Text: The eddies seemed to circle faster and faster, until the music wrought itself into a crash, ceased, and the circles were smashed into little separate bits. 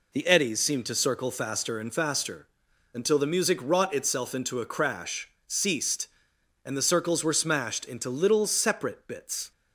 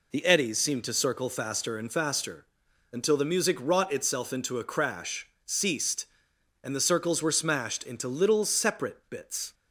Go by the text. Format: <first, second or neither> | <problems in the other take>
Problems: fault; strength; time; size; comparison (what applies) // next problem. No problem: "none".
neither | none